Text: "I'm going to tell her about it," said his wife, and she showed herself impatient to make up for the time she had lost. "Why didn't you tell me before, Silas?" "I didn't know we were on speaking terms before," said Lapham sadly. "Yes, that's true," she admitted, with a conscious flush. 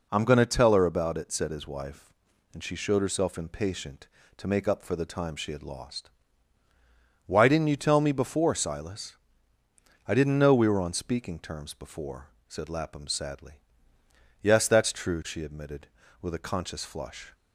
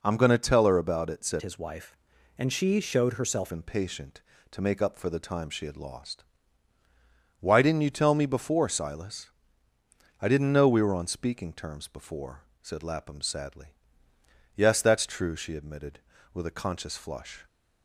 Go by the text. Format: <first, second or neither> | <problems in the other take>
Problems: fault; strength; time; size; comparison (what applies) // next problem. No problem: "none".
first | changes voice from "his" to "herself"; from 1.4 to 3.5 s; 2.1 s long